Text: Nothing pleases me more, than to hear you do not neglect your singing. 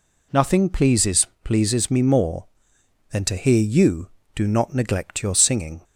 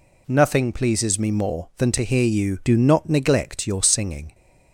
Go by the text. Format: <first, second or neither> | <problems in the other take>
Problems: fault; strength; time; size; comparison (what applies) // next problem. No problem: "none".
second | says "pleases" twice; at 1.4 s